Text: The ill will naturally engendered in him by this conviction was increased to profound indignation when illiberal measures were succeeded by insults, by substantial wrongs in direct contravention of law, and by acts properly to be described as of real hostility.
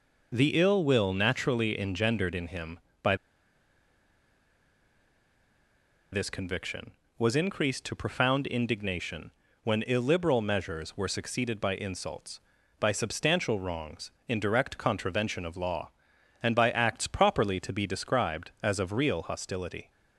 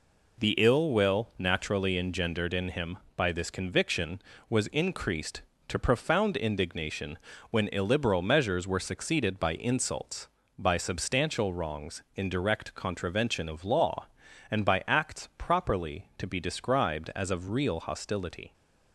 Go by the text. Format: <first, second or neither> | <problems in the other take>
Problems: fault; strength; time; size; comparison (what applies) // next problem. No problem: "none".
second | pauses between "by" and "this"; strong; at 3.1 s; 2.9 s long // pauses between "indignation" and "when"; slight; at 9.3 s; 0.32 s long; slight in the second